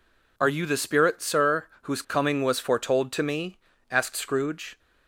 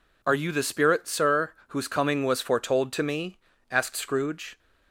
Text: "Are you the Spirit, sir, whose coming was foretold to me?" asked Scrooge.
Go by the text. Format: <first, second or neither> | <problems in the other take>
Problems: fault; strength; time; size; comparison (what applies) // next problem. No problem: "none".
neither | none